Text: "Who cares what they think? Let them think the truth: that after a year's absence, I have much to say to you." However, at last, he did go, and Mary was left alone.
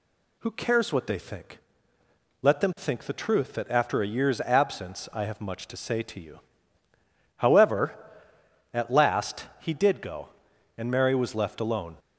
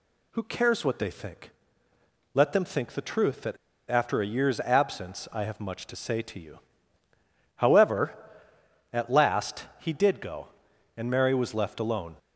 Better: first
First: none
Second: pauses between "that" and "after"; slight; at 3.5 s; 0.32 s long

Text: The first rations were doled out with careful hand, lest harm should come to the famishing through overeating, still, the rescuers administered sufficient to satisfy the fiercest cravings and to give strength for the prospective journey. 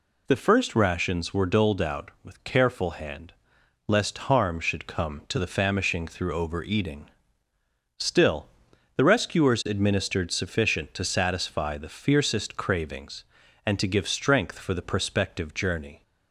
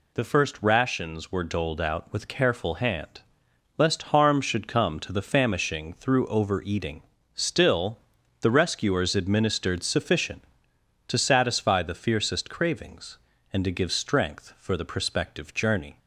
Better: neither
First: none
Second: none

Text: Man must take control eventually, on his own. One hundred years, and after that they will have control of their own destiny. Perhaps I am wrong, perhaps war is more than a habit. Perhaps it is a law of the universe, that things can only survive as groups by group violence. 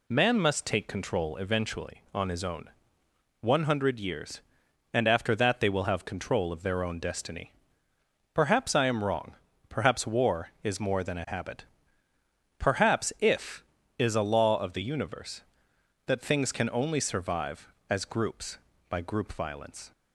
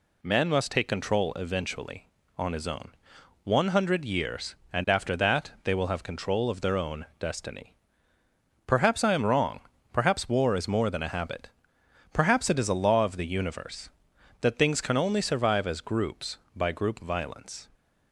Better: second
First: says "if" for "it"; at 13.1 s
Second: none

